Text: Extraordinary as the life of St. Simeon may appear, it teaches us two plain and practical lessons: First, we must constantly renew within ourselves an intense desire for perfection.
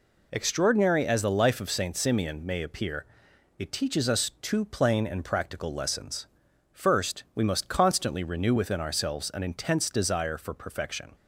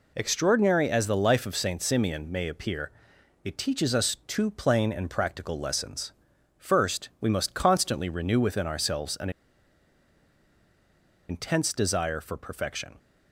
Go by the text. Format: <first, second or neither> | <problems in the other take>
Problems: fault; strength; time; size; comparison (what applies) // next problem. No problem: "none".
first | pauses between "an" and "intense"; strong; at 9.2 s; 1.9 s long